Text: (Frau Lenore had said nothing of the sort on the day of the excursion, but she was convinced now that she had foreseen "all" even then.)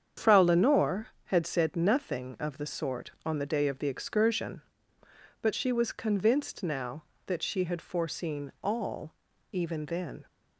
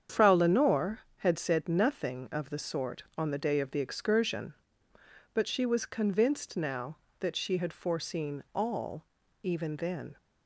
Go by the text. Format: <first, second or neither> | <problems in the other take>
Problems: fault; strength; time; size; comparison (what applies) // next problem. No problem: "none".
neither | starts louder than the rest; strong; the same in both // pauses between "all" and "even"; the same in both